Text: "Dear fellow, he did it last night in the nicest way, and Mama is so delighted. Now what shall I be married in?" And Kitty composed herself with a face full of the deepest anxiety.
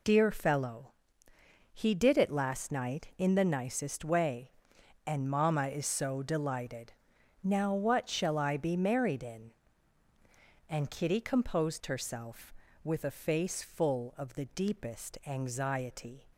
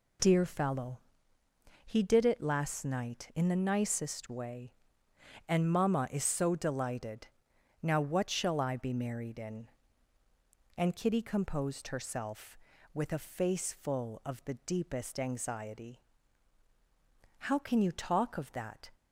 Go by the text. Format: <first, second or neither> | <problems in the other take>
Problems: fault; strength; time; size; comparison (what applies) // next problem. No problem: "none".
first | goes on to say "How can you talk of that"; from 17.3 s on; 1.5 s long